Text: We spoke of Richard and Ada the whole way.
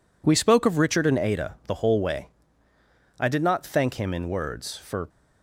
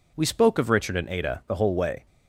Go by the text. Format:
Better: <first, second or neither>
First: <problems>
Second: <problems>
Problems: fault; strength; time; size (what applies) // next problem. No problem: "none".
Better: second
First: goes on to say "I did not thank him in words for"; strong; from 3.2 s on; 1.8 s long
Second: none